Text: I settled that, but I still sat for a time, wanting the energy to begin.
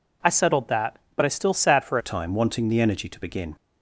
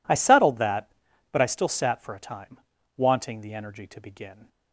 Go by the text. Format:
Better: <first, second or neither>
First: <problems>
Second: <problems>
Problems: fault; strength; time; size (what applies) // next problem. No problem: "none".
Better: second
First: changes voice at "a"; from 2.0 s on; 1.5 s long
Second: none